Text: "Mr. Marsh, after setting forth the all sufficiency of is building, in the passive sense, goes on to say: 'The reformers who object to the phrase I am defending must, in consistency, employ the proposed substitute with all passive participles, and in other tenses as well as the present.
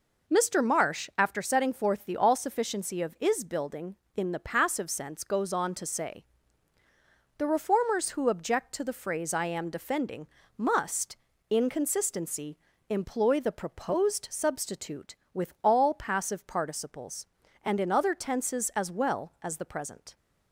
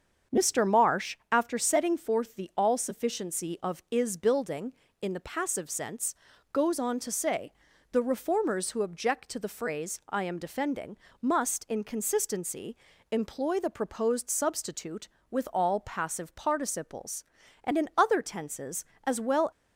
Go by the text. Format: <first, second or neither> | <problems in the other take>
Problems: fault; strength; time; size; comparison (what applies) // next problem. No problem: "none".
first | starts louder than the rest; strong; until 1.4 s; 7 dB // pauses between "defending" and "must"; slight; at 10.9 s; 0.24 s long; slight in the first // stops before "as the present"; at 19.5 s